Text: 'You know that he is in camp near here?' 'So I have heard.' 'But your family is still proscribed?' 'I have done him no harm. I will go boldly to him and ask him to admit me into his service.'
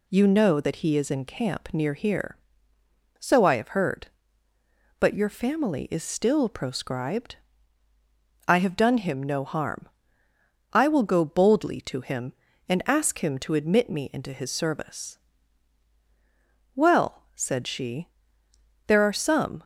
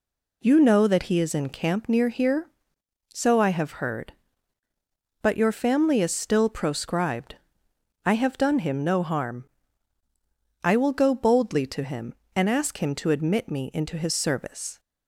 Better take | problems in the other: second | goes on to say "Well said she there are some"; strong; from 16.7 s on; 2.8 s long

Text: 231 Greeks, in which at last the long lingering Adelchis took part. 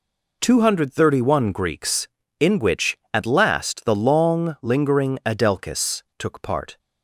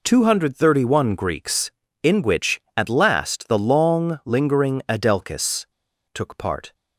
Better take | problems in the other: first | pauses between "Adelchis" and "took"; noticeable; at 5.6 s; 0.46 s long

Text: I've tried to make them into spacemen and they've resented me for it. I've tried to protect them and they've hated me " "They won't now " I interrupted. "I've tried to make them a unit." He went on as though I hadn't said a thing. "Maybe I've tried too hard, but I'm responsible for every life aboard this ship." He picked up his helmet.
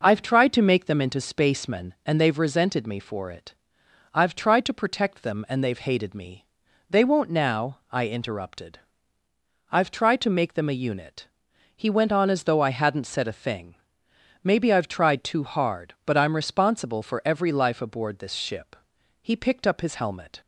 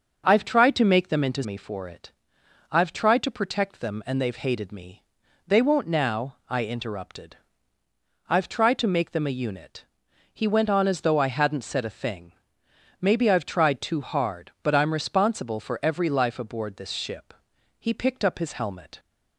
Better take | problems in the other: first | starts louder than the rest; until 1.2 s; 7 dB; also in the first // skips "spacemen and they've resented"; at 1.4 s

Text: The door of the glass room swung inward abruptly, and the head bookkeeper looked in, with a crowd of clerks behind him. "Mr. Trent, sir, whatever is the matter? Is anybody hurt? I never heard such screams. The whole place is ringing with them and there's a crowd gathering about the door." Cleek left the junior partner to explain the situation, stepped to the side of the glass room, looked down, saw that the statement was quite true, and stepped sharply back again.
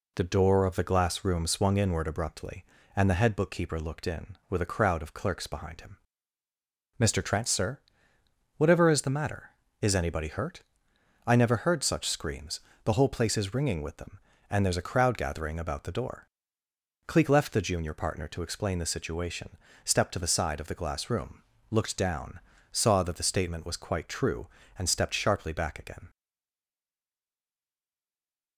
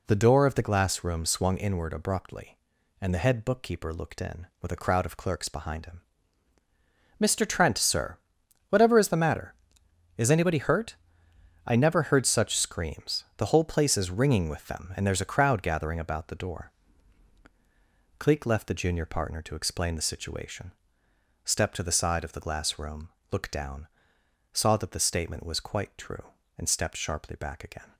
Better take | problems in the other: second | stays silent after the last word; from 26.0 s on; 2.5 s long

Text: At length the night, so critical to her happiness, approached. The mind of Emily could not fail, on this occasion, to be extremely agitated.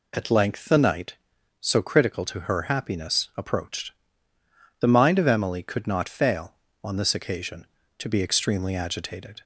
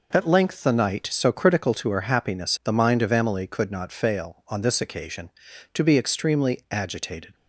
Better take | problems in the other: first | skips "approached"; at 2.6 s

